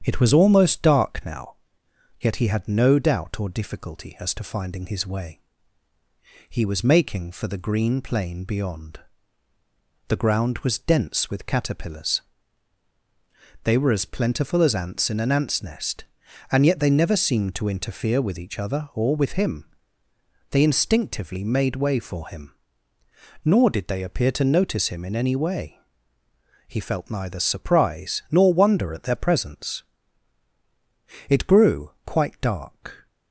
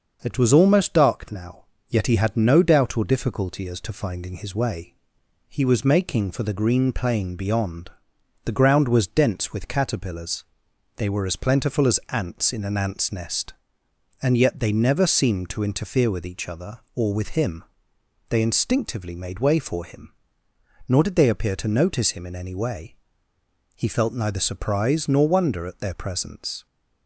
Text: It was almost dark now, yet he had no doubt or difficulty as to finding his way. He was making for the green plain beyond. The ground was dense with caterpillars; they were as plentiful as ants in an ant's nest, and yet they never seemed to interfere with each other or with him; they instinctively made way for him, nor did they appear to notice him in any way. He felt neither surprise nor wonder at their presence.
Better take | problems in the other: second | starts louder than the rest; strong; until 1.0 s; 8.5 dB; also in the second // goes on to say "It grew quite dark"; strong; from 31.2 s on; 1.7 s long

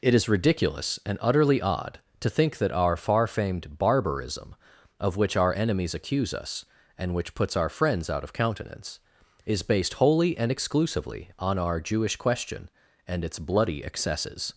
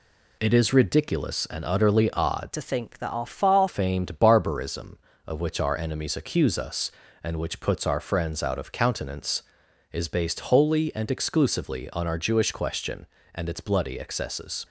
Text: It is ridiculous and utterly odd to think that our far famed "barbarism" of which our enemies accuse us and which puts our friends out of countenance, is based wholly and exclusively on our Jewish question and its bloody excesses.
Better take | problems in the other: first | changes voice from "to" to "far"; from 2.5 to 3.6 s; 1.1 s long

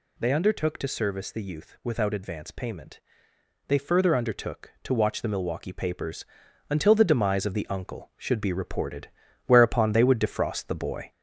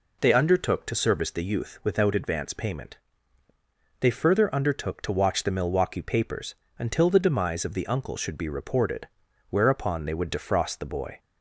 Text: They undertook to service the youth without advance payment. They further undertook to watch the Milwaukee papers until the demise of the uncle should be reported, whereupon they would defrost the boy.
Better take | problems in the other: second | gets louder; throughout; 3.5 dB // pauses between "papers" and "until"; noticeable; at 6.2 s; 0.46 s long; slight in the second

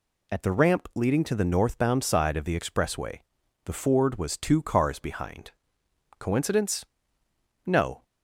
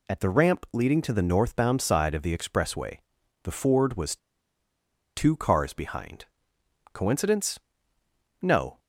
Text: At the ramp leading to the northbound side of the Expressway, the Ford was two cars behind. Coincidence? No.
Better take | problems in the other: first | pauses between "was" and "two"; at 4.1 s; 0.98 s long

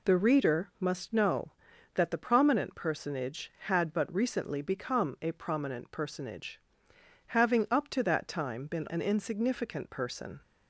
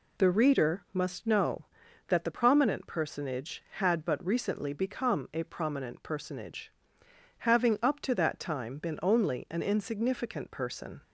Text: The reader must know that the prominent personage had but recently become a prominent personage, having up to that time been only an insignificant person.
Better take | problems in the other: second | skips "only"; at 8.8 s

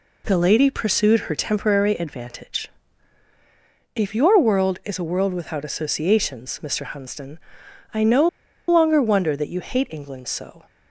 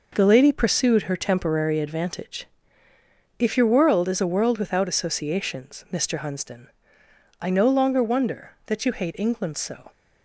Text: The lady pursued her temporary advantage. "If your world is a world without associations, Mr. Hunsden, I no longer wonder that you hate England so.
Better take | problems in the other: second | pauses between "no" and "longer"; at 8.2 s; 0.40 s long

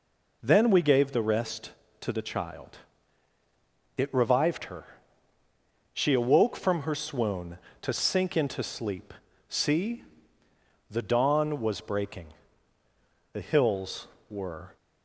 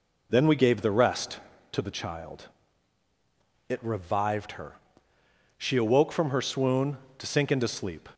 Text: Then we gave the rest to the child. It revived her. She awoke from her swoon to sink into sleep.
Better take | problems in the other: second | goes on to say "See the dawn was breaking The hills were"; strong; from 9.4 s on; 5.2 s long

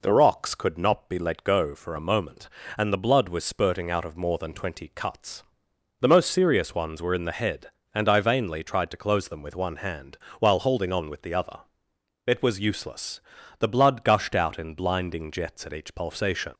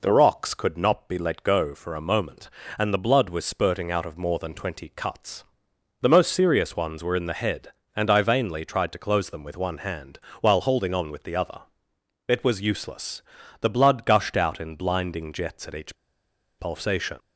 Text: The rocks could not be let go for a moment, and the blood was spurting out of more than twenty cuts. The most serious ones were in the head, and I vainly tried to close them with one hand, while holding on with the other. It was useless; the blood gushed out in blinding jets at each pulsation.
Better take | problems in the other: first | pauses between "each" and "pulsation"; noticeable; at 15.9 s; 0.63 s long

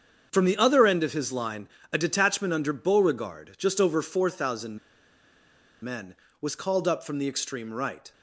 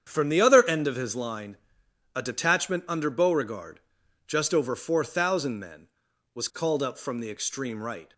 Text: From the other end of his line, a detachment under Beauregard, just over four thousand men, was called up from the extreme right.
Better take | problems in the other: second | starts louder than the rest; strong; until 1.3 s; 7 dB; strong in the second // pauses between "thousand" and "men"; at 4.7 s; 1.0 s long

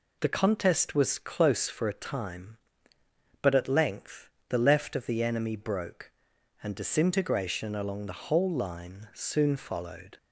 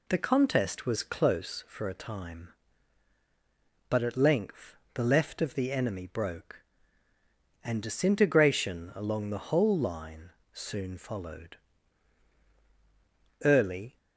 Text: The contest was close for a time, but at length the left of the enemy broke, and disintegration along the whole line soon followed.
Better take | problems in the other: first | pauses between "length" and "the"; slight; at 4.7 s; 0.18 s long; slight in the first // pauses between "line" and "soon"; slight; at 10.2 s; 0.24 s long // goes on to say "Early"; from 13.4 s on; 0.54 s long

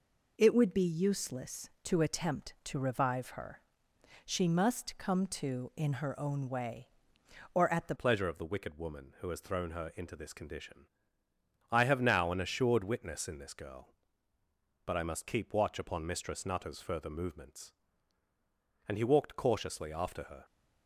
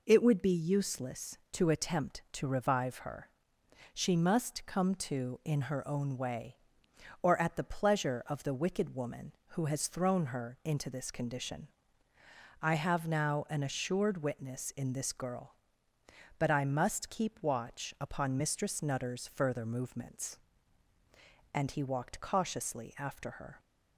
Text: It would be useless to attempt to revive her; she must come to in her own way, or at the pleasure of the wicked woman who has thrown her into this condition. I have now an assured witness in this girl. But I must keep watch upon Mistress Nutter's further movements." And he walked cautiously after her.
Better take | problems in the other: second | changes voice at "pleasure"; from 7.9 s on; 12.5 s long

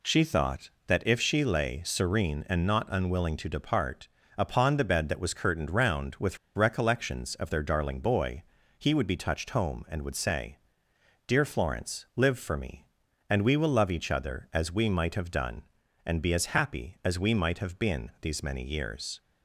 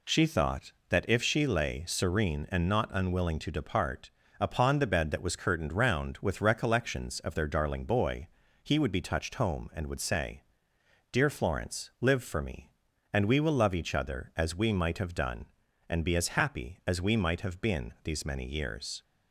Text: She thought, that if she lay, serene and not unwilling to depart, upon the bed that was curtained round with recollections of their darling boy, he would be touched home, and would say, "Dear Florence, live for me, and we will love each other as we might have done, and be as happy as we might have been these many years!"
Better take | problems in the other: second | pauses between "with" and "recollections"; slight; at 6.3 s; 0.18 s long

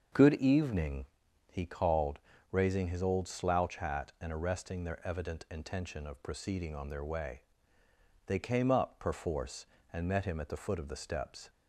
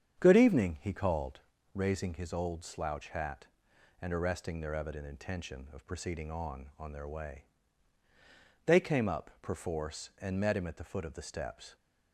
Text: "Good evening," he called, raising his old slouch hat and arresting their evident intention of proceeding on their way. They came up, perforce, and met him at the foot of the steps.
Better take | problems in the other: first | starts louder than the rest; strong; until 1.2 s; 8 dB; also in the first // says "on" twice; at 6.7 s

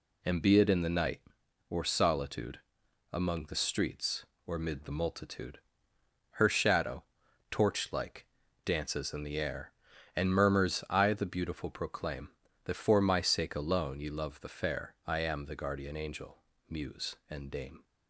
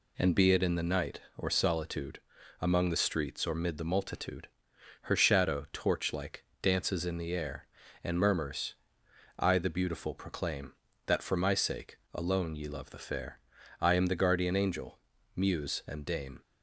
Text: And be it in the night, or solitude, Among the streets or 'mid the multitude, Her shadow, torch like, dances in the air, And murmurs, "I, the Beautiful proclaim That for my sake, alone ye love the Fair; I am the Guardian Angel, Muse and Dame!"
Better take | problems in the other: neither | none

